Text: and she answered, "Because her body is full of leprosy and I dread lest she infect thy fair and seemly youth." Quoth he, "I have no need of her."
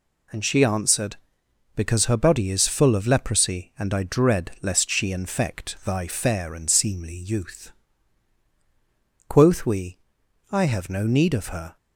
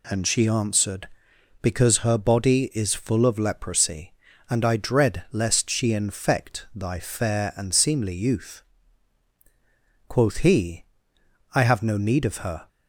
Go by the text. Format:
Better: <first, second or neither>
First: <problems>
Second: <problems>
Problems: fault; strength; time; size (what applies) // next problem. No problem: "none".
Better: second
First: says "we" for "he"; at 9.6 s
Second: none